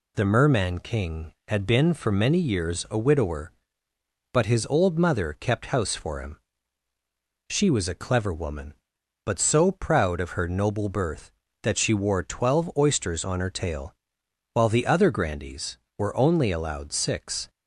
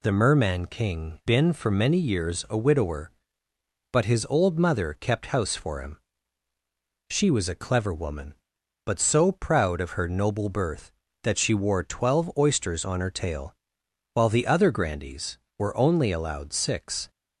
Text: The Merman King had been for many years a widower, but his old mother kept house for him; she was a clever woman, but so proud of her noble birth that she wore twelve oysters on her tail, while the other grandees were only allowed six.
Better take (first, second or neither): first